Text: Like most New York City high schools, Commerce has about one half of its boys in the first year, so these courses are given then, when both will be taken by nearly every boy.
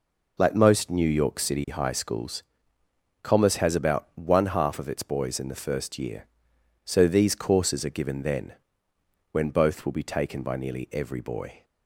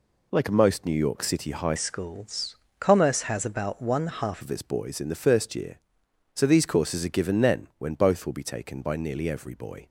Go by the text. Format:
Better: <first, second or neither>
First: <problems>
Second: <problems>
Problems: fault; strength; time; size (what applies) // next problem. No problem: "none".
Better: first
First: none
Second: changes voice from "schools" to "half"; from 1.7 to 4.4 s; 2.7 s long